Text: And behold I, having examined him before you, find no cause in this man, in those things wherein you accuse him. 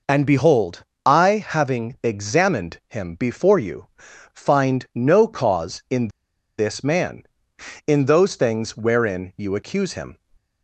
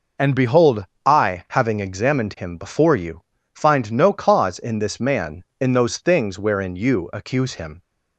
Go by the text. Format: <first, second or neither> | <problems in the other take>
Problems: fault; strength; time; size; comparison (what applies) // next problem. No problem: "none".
second | pauses between "behold" and "I"; slight; at 0.8 s; 0.22 s long; slight in the second // pauses between "in" and "this"; noticeable; at 6.0 s; 0.49 s long